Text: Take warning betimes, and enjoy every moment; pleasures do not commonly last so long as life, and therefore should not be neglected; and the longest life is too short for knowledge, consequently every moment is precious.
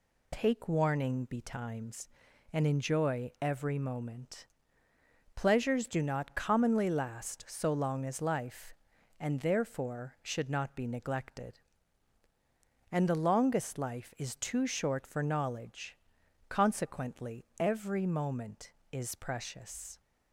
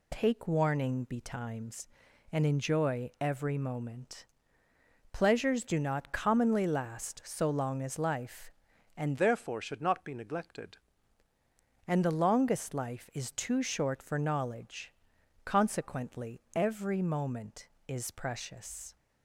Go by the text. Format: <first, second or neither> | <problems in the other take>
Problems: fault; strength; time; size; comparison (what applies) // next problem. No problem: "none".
first | changes voice from "therefore" to "neglected"; from 9.1 to 10.7 s; 1.6 s long